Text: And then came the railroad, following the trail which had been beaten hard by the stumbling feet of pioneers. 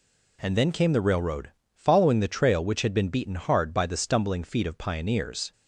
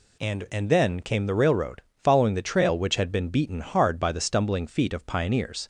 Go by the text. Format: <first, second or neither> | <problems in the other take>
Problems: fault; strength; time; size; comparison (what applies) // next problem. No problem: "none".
first | says "And" twice; at 0.4 s